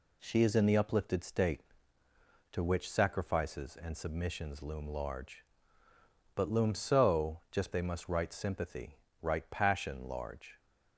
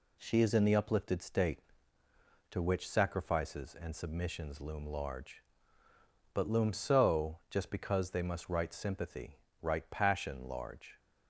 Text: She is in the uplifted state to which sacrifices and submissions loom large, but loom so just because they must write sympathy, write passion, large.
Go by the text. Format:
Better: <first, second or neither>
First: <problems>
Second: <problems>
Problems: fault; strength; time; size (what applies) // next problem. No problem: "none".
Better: second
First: skips "because"; at 7.7 s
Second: none